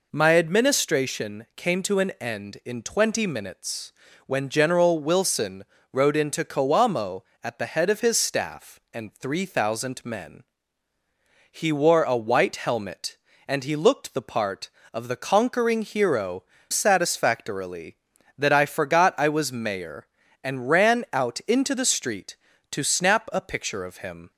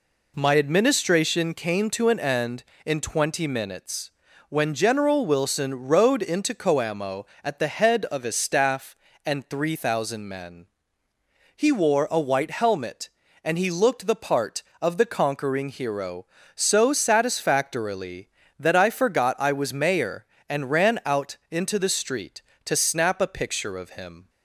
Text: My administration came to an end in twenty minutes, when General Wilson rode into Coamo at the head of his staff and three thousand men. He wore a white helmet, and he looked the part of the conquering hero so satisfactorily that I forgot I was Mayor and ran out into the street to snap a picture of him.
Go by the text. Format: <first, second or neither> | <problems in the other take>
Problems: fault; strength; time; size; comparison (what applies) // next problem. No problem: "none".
second | pauses between "Wilson" and "rode"; slight; at 5.6 s; 0.28 s long // skips "so"; at 16.5 s